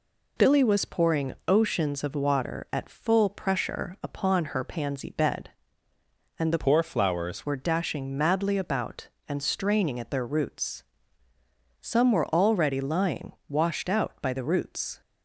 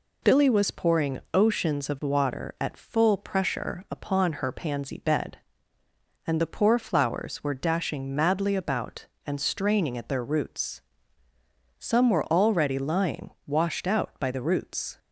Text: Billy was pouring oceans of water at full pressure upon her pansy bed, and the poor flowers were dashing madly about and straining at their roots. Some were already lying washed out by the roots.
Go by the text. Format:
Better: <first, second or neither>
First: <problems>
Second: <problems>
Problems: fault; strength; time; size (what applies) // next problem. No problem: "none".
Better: second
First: pauses between "pouring" and "oceans"; slight; at 1.3 s; 0.16 s long // changes voice from "poor" to "flowers"; from 6.5 to 7.4 s; 0.9 s long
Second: pauses between "pouring" and "oceans"; slight; at 1.1 s; 0.16 s long